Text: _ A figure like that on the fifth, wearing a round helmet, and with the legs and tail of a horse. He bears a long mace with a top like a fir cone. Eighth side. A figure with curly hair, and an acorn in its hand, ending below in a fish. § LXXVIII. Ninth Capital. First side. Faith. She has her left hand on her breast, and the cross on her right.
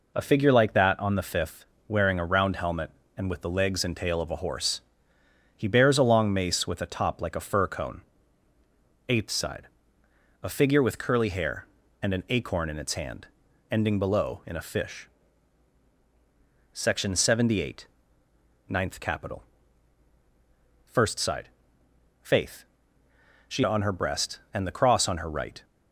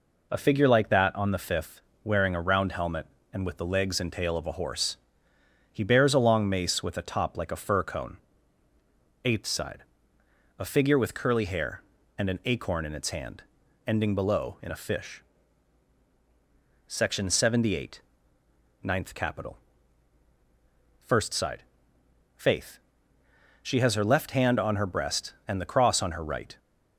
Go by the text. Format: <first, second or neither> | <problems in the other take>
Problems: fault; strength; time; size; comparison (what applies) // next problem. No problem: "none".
second | skips "has her left hand"; at 23.6 s